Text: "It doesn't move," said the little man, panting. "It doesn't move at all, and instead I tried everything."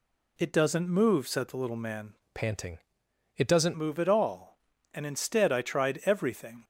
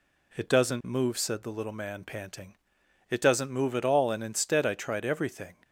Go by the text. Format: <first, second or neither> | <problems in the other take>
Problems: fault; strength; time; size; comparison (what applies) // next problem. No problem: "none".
second | changes voice from "panting" to "doesn't"; from 2.3 to 3.7 s; 1.4 s long